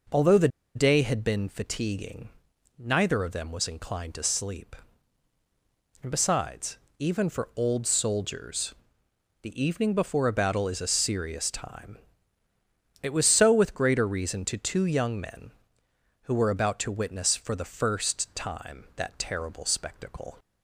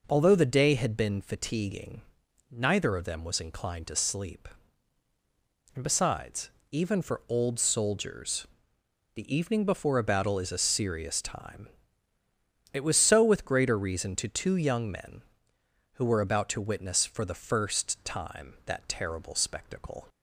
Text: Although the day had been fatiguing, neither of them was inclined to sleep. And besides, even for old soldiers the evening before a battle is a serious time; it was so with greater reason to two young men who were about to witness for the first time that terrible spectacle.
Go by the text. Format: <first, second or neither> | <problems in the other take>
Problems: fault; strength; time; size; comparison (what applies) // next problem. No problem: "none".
second | pauses between "the" and "day"; slight; at 0.4 s; 0.27 s long // pauses between "soldiers" and "the"; noticeable; at 8.7 s; 0.70 s long; noticeable in the second